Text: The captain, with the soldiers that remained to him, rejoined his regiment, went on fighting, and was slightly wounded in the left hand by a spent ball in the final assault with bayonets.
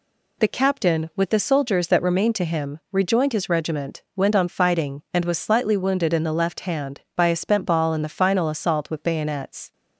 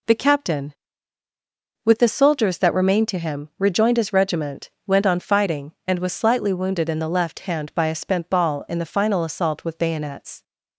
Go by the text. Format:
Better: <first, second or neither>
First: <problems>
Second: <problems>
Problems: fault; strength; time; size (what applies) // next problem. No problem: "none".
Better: neither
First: none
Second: none